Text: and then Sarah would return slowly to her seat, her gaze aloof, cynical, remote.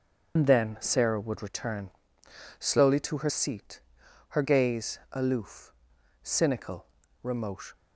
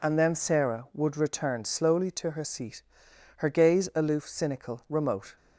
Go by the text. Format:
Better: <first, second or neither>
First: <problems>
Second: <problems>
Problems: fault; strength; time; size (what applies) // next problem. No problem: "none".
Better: second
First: loses the start of "and"; at 0.3 s; 70 ms // starts louder than the rest; until 1.3 s; 6.5 dB // pauses between "return" and "slowly"; noticeable; at 1.8 s; 0.70 s long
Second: none